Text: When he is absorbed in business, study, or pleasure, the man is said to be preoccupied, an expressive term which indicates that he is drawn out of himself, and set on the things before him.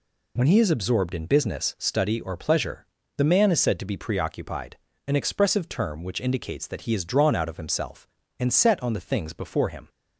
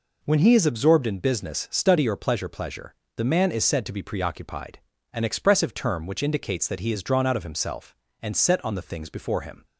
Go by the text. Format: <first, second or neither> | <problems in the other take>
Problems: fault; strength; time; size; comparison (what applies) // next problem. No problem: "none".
first | says "pleasure" twice; at 2.4 s